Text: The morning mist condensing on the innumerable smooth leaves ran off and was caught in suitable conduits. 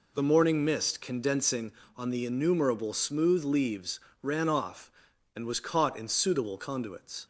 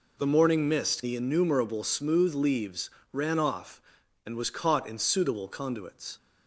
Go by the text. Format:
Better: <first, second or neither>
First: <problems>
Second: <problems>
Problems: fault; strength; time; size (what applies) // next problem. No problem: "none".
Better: first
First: pauses between "leaves" and "ran"; slight; at 3.9 s; 0.24 s long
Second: skips "condensing on"; at 1.0 s // pauses between "leaves" and "ran"; slight; at 2.8 s; 0.24 s long